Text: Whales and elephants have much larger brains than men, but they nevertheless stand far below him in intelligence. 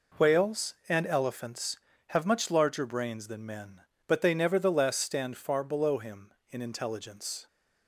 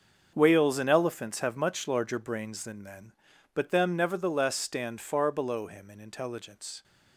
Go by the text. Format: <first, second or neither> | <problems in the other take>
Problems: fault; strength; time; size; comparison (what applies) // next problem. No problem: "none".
first | starts louder than the rest; until 1.3 s; 6.5 dB // says "them" for "they"; at 3.6 s